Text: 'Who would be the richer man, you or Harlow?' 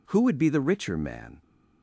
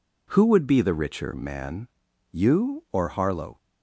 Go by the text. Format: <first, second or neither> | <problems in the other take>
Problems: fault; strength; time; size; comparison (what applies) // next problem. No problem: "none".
second | stops before "you or Harlow"; at 1.4 s